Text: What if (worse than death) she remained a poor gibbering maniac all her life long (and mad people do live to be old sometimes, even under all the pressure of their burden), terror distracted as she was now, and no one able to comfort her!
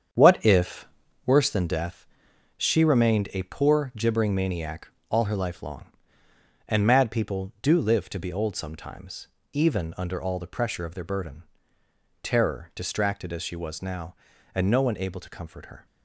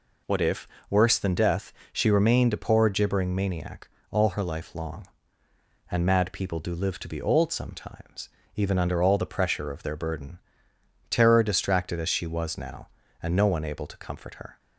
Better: second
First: starts louder than the rest; strong; until 1.3 s; 8 dB // pauses between "maniac" and "all"; slight; at 4.8 s; 0.20 s long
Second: pauses between "maniac" and "all"; slight; at 3.8 s; 0.20 s long

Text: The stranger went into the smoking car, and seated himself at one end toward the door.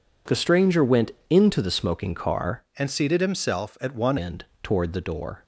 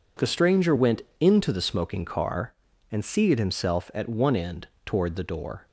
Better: second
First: pauses between "went" and "into"; slight; at 1.1 s; 0.16 s long // changes voice from "and" to "one"; from 2.7 to 4.1 s; 1.4 s long // pauses between "end" and "toward"; slight; at 4.4 s; 0.16 s long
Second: pauses between "went" and "into"; slight; at 1.0 s; 0.16 s long // pauses between "end" and "toward"; slight; at 4.6 s; 0.16 s long

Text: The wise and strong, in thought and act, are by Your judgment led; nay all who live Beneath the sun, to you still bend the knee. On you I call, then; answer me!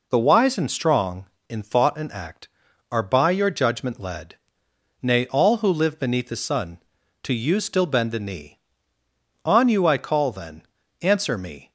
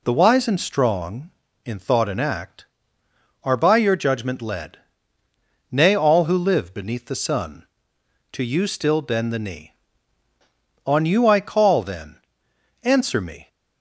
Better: neither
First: none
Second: none

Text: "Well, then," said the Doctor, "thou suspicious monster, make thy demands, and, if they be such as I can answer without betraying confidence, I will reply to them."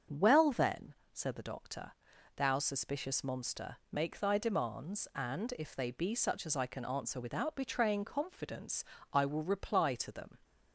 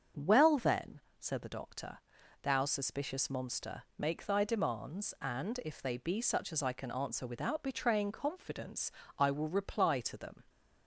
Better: neither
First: starts louder than the rest; until 1.2 s; 6.5 dB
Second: starts louder than the rest; until 1.3 s; 6.5 dB

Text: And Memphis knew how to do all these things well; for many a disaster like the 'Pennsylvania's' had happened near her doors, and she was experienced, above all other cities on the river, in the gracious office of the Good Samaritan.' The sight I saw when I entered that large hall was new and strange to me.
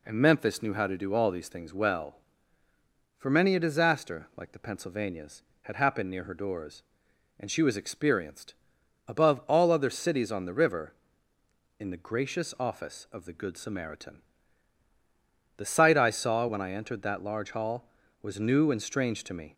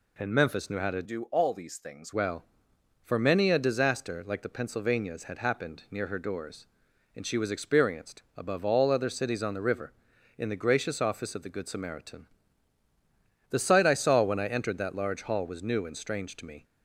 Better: first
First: none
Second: changes voice from "do" to "things"; from 1.0 to 2.1 s; 1.1 s long

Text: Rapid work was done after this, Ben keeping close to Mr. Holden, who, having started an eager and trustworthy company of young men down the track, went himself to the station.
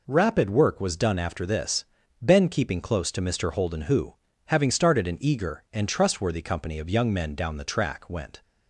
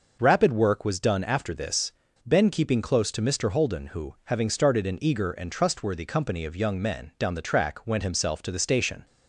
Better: second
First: stops before "himself to the station"; at 8.4 s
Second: none

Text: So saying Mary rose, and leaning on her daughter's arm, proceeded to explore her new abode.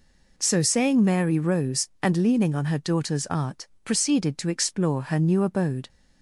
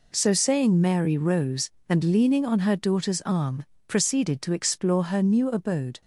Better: second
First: says "art" for "arm"; at 3.2 s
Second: none

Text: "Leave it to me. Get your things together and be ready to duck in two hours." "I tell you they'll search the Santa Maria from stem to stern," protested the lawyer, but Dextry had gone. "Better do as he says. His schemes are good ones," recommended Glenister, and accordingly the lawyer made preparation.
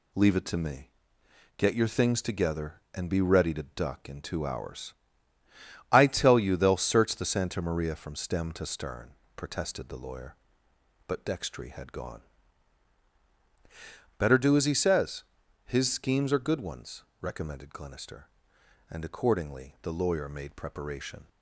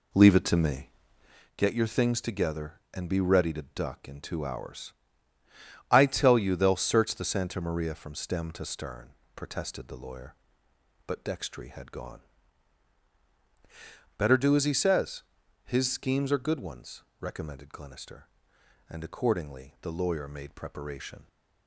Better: first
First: none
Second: starts louder than the rest; slight; until 1.5 s; 2.5 dB

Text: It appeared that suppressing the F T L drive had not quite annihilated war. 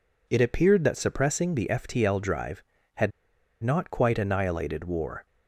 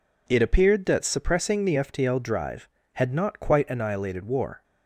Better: second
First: pauses between "had" and "not"; noticeable; at 3.1 s; 0.52 s long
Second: none

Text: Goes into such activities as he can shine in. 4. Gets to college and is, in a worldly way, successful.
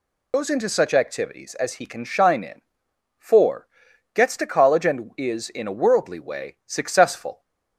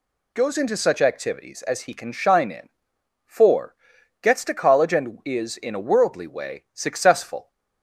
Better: second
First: loses the start of "Goes"; at 0.3 s; 75 ms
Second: none

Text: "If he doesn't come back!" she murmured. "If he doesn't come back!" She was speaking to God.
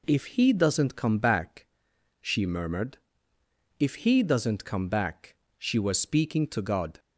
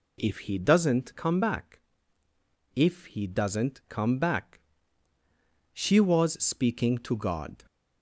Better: first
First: none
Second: skips "she murmured"; at 2.2 s

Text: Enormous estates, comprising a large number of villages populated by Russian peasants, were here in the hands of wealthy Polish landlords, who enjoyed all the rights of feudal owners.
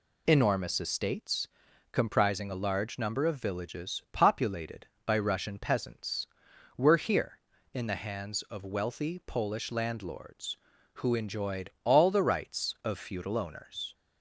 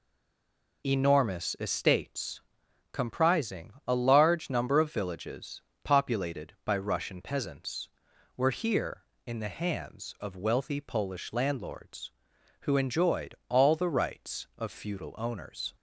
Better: first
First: none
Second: stays silent before the first word; slight; until 0.8 s; 0.8 s long // pauses between "villages" and "populated"; slight; at 5.6 s; 0.22 s long

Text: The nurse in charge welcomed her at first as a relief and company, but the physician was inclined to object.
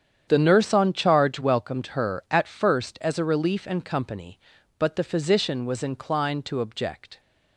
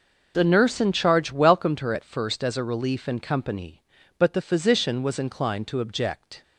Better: second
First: starts louder than the rest; strong; until 1.3 s; 8.5 dB // says "on" for "in"; at 0.7 s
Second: none

